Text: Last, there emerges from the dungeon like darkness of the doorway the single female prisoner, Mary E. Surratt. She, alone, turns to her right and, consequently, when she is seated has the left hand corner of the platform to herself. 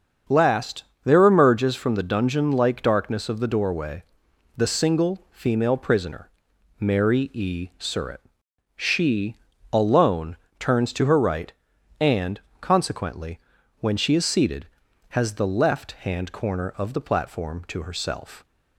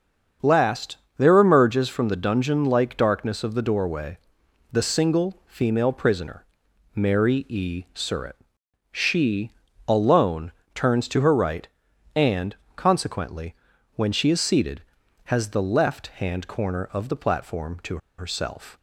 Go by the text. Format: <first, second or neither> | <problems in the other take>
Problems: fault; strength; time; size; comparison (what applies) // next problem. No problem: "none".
first | starts louder than the rest; until 1.6 s; 7 dB; also in the first // pauses between "doorway" and "the"; noticeable; at 4.1 s; 0.52 s long; noticeable in the first // pauses between "to" and "herself"; slight; at 17.9 s; 0.20 s long